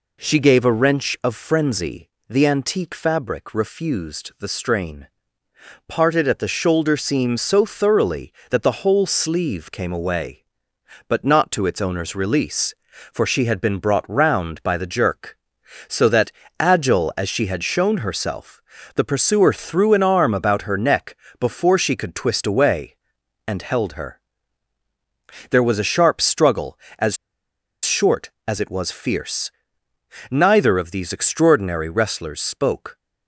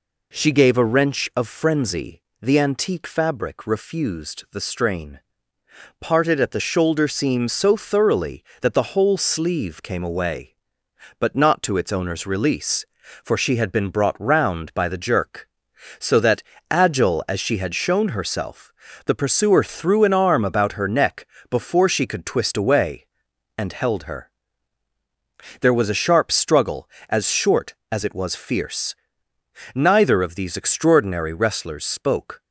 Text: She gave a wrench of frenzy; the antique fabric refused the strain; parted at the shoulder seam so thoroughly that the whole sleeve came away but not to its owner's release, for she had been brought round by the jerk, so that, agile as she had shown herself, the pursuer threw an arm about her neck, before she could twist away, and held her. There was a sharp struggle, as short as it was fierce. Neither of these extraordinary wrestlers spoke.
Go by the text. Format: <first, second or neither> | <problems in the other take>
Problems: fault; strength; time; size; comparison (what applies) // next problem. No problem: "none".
second | pauses between "as" and "short"; noticeable; at 27.1 s; 0.69 s long